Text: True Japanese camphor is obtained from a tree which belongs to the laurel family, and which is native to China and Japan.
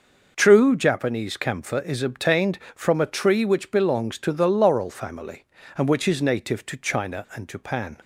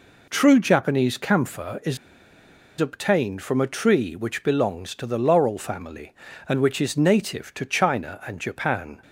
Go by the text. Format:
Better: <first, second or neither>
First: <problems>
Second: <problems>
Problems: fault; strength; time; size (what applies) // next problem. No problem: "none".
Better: first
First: none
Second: pauses between "is" and "obtained"; noticeable; at 1.9 s; 0.82 s long